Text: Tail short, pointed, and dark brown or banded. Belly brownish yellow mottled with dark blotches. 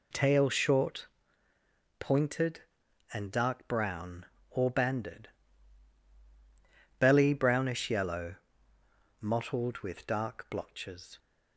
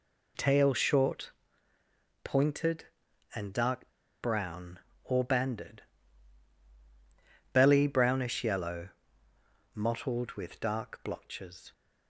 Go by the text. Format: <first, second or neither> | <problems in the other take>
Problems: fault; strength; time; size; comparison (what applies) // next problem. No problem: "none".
first | pauses between "dark" and "brown"; slight; at 3.8 s; 0.33 s long // pauses between "yellow" and "mottled"; noticeable; at 8.9 s; 0.84 s long; noticeable in the first